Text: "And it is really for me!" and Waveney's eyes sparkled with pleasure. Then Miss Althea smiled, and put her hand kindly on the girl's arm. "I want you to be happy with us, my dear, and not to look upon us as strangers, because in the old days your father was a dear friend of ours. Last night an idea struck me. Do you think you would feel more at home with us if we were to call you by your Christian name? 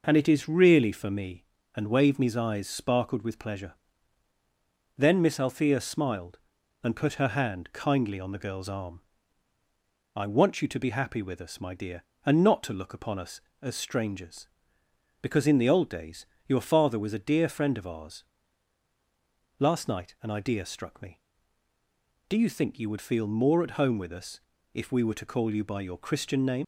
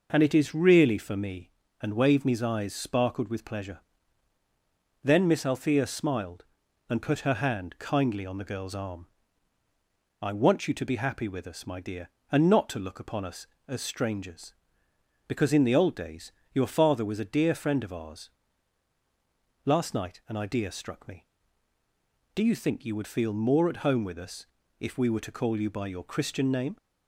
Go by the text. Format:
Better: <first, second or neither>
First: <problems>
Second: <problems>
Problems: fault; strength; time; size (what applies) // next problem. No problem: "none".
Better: second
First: pauses between "days" and "your"; slight; at 16.2 s; 0.20 s long // pauses between "us" and "if"; slight; at 24.3 s; 0.36 s long // leaves "name" unfinished; at 26.6 s; 60 ms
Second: pauses between "days" and "your"; slight; at 16.3 s; 0.20 s long // pauses between "us" and "if"; slight; at 24.4 s; 0.36 s long